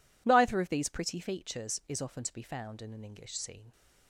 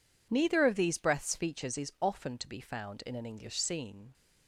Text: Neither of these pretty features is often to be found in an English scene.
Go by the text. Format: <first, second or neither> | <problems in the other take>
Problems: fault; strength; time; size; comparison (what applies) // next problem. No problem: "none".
first | says "breaths" for "pretty"; at 0.9 s